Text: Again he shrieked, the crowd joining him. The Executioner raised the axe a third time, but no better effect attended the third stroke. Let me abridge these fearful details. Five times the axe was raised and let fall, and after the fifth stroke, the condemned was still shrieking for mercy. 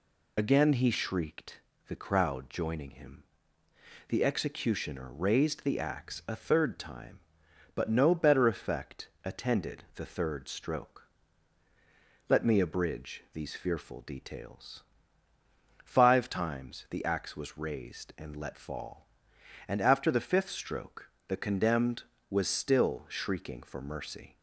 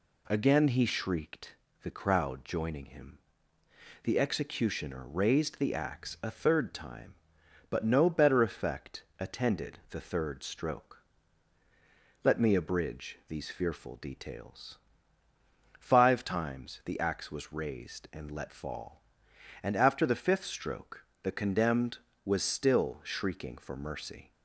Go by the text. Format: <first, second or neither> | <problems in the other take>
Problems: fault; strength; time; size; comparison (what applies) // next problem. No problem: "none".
second | loses the start of "Again"; at 0.3 s; 65 ms // pauses between "effect" and "attended"; slight; at 9.0 s; 0.16 s long; slight in the second